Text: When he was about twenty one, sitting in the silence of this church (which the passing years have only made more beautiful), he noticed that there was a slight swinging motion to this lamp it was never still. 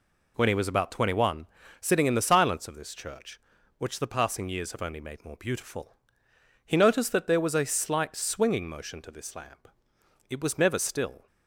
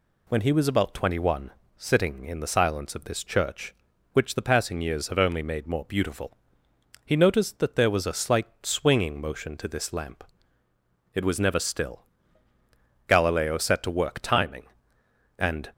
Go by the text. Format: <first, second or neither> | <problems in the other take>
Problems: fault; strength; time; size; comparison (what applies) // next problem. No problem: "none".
first | pauses between "slight" and "swinging"; slight; at 8.4 s; 0.16 s long // pauses between "lamp" and "it"; noticeable; at 10.2 s; 0.90 s long; noticeable in the first // goes on to say "Galileo set to work timing and"; strong; from 13.0 s on; 2.6 s long